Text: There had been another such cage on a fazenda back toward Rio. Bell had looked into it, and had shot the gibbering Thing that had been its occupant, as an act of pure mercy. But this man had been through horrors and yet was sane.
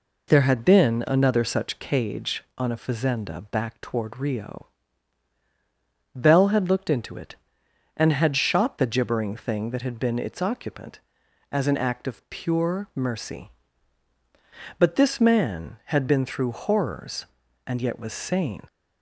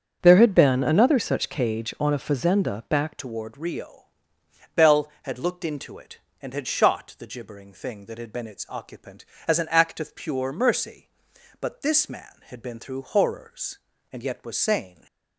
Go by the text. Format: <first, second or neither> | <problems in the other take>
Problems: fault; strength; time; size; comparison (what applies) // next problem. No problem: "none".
first | starts louder than the rest; strong; until 1.2 s; 7 dB // changes voice at "toward"; from 3.1 s on; 11.9 s long